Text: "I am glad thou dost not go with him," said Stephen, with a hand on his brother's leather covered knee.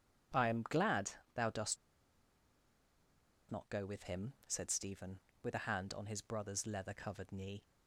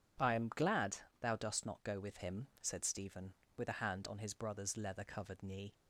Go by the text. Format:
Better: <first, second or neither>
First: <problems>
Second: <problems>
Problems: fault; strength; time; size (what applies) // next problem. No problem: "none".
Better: second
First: pauses between "glad" and "thou"; slight; at 1.1 s; 0.24 s long // pauses between "dost" and "not"; strong; at 1.7 s; 1.7 s long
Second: pauses between "glad" and "thou"; slight; at 0.9 s; 0.24 s long